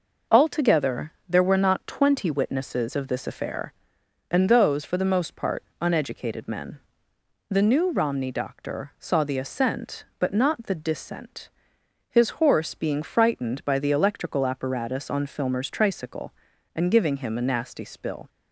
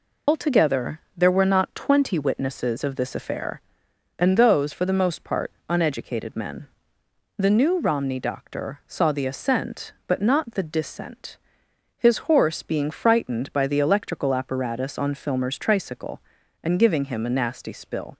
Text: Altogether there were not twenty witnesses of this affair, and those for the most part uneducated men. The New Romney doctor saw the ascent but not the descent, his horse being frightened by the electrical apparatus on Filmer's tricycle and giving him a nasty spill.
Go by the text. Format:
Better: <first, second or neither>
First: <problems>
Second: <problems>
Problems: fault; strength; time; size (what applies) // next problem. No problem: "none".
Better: first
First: pauses between "Altogether" and "there"; slight; at 1.1 s; 0.16 s long // pauses between "part" and "uneducated"; slight; at 5.6 s; 0.18 s long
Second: loses the start of "Altogether"; at 0.2 s; 95 ms // pauses between "Altogether" and "there"; slight; at 1.0 s; 0.16 s long // pauses between "part" and "uneducated"; slight; at 5.5 s; 0.18 s long